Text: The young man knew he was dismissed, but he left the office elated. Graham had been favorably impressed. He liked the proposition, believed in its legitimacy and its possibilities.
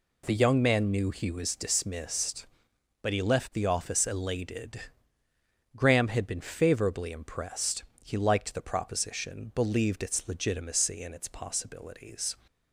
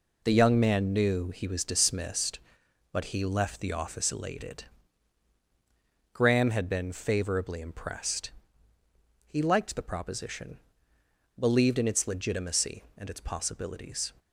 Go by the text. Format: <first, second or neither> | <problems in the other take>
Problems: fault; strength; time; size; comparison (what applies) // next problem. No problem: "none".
second | skips "in"; at 10.0 s